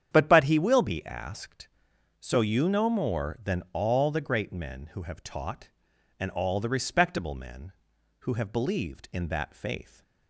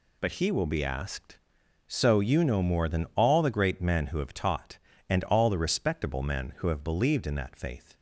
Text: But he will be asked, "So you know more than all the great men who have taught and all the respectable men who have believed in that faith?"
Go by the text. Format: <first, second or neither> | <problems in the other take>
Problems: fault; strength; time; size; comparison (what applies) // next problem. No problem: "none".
second | starts louder than the rest; strong; until 1.1 s; 9 dB // says "But" twice; at 0.2 s